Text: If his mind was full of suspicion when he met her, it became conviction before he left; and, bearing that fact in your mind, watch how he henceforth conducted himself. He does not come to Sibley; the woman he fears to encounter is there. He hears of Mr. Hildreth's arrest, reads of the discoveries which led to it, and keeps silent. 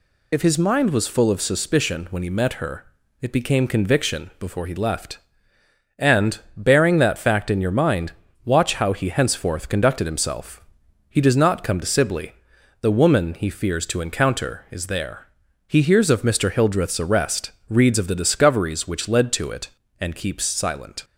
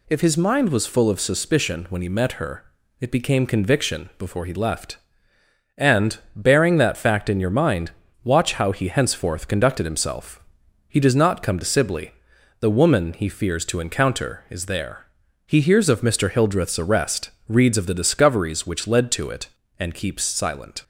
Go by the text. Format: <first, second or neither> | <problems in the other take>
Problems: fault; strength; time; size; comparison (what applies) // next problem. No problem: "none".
second | loses the start of "If"; at 0.3 s; 45 ms